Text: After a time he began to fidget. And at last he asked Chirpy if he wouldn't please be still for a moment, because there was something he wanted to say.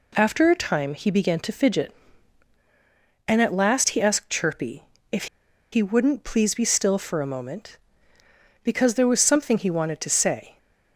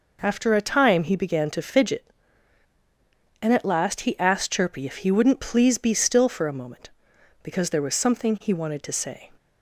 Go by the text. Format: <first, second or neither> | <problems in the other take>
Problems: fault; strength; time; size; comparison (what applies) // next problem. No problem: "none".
second | pauses between "Chirpy" and "if"; slight; at 4.8 s; 0.28 s long // pauses between "if" and "he"; noticeable; at 5.2 s; 0.46 s long